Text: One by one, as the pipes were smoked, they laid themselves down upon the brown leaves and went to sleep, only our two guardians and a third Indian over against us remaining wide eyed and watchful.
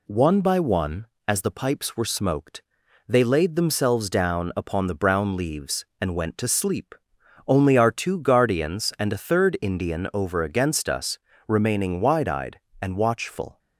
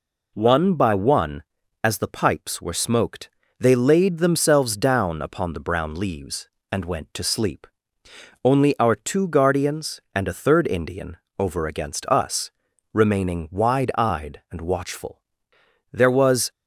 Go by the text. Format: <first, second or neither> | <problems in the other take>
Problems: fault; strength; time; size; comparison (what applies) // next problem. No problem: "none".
first | pauses between "Indian" and "over"; slight; at 11.1 s; 0.20 s long // pauses between "us" and "remaining"; at 12.5 s; 0.42 s long; slight in the first // goes on to say "There was"; from 15.9 s on; 0.58 s long